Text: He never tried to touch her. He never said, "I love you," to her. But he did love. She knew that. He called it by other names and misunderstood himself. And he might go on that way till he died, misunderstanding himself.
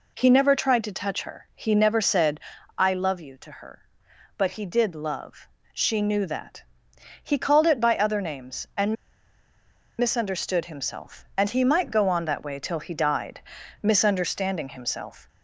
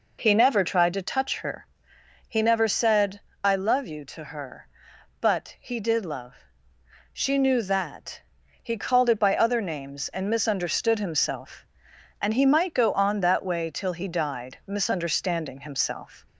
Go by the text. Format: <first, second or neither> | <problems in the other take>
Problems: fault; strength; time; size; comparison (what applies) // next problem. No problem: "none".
second | pauses between "and" and "misunderstood"; at 8.9 s; 1.0 s long